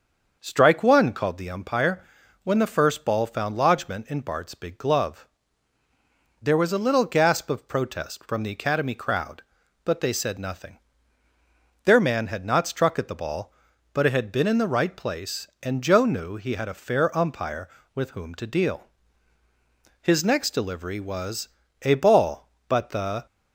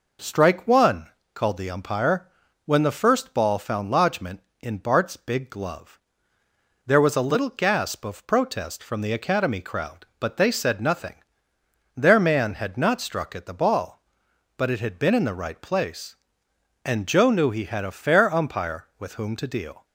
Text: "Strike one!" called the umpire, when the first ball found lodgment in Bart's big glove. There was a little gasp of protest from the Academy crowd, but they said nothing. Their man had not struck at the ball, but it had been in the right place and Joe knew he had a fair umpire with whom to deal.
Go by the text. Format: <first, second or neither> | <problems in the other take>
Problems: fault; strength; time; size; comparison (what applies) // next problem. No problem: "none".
second | starts louder than the rest; until 1.4 s; 6.5 dB // goes on to say "His next delivery was a ball but the"; strong; from 20.0 s on; 3.2 s long